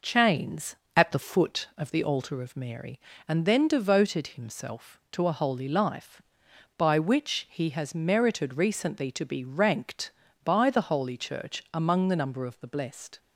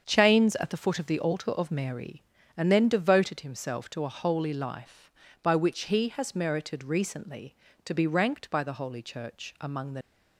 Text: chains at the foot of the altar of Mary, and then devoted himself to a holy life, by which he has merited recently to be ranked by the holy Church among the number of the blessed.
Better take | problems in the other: first | starts louder than the rest; strong; until 1.0 s; 7 dB // stops before "number of the blessed"; at 10.0 s

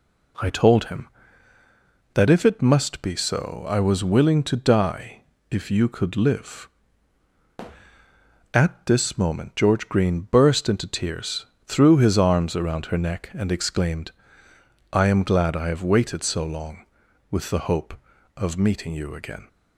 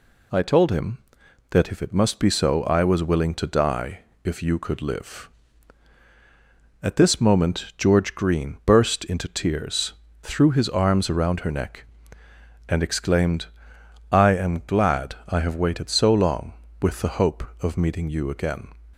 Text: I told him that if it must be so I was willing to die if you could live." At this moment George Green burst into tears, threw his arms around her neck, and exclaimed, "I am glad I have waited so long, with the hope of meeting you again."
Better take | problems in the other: neither | pauses between "die" and "if"; slight; the same in both

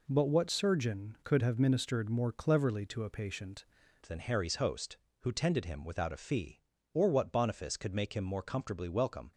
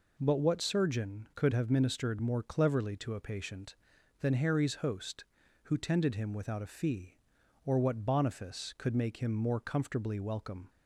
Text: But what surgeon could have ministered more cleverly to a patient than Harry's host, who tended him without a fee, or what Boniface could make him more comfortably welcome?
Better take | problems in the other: second | changes voice at "than"; from 4.0 s on; 5.3 s long

